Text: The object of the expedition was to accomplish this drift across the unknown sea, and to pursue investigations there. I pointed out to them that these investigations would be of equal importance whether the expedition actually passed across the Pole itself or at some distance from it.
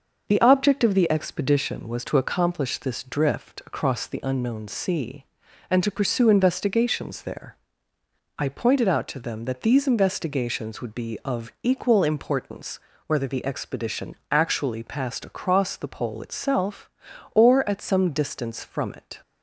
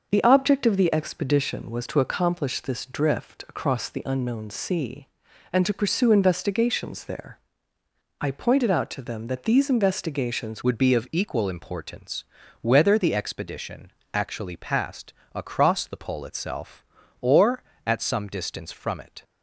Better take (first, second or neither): first